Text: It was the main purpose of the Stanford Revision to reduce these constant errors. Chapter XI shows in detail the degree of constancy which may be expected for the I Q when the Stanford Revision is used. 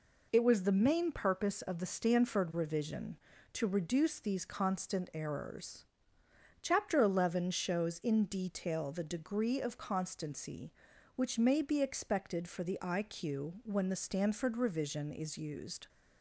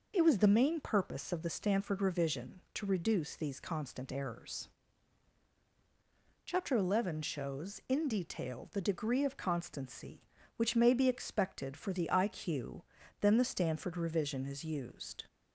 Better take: first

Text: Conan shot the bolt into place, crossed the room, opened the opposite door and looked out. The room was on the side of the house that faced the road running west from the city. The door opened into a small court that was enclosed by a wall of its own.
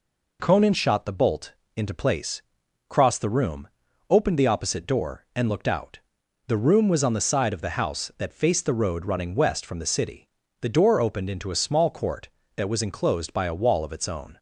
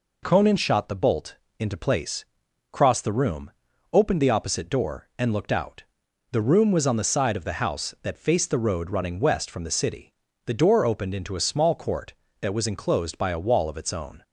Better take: neither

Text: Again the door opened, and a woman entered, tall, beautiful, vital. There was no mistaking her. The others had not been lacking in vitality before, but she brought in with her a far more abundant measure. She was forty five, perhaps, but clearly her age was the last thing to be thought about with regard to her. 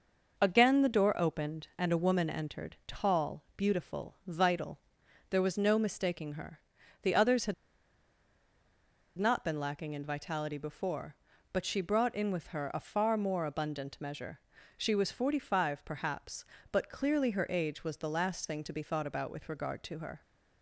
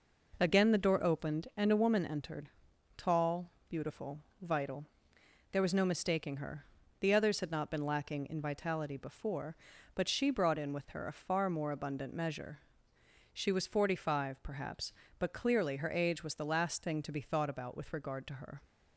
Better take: second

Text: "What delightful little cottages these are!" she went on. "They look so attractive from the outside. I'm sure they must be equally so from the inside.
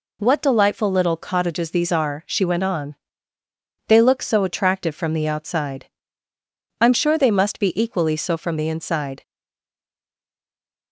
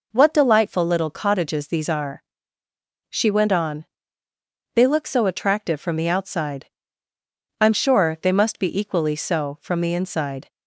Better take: second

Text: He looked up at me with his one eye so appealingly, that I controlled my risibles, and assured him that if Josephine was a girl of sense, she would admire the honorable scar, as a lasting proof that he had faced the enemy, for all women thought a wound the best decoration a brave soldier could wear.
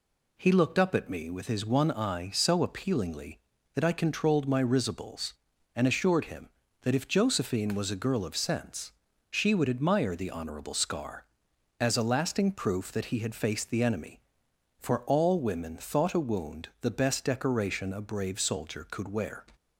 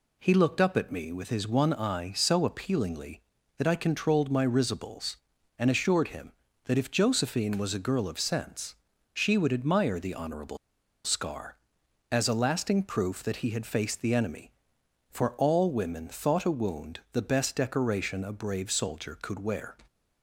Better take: first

